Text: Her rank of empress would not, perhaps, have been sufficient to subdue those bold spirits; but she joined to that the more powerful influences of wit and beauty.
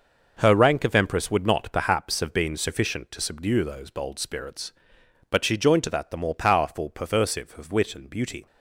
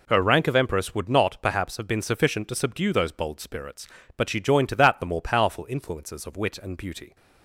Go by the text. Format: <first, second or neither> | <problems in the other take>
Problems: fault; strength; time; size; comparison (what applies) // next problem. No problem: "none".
second | says "perversive" for "influences"; at 6.9 s